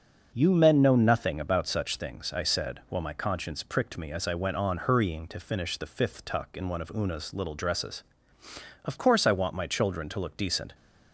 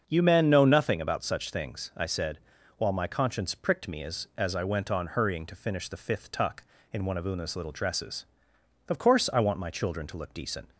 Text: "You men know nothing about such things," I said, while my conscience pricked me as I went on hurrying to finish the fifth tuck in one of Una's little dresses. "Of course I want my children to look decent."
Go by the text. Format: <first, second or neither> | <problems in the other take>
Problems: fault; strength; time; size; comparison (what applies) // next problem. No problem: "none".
first | starts louder than the rest; until 1.0 s; 6.5 dB; also in the first // says "as" twice; at 4.3 s